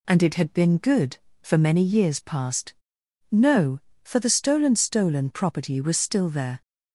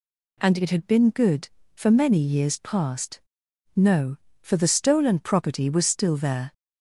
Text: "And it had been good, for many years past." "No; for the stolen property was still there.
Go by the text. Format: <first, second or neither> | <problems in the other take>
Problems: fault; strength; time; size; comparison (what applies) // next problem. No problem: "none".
second | says "stolen" twice; at 4.7 s